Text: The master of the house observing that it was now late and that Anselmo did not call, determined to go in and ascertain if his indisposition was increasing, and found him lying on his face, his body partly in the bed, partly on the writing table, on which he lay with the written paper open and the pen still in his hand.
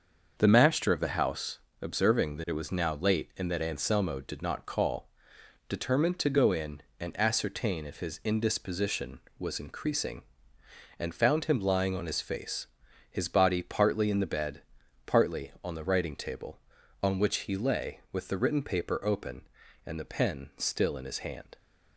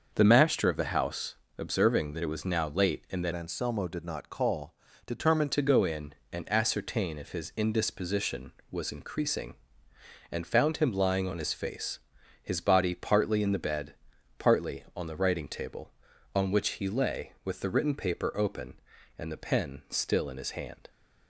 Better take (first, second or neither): first